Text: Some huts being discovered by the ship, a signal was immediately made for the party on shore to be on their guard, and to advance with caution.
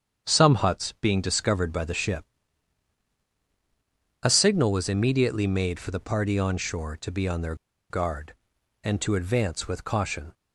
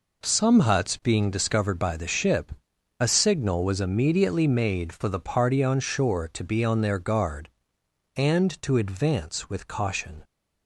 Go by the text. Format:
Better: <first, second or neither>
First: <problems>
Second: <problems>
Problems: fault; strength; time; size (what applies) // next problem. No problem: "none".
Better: second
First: starts louder than the rest; strong; until 1.3 s; 8 dB // pauses between "their" and "guard"; slight; at 7.5 s; 0.35 s long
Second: none